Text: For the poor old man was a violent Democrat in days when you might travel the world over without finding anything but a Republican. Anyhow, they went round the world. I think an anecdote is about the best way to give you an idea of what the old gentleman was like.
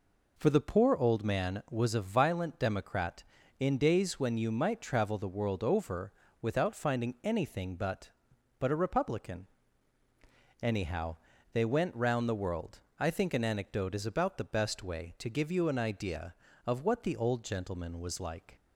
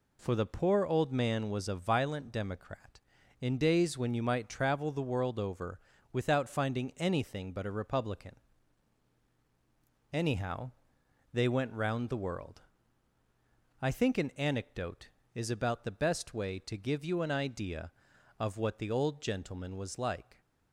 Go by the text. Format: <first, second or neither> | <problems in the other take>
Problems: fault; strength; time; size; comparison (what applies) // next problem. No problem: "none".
second | pauses between "over" and "without"; slight; at 6.1 s; 0.30 s long; slight in the second // says "but" twice; at 8.5 s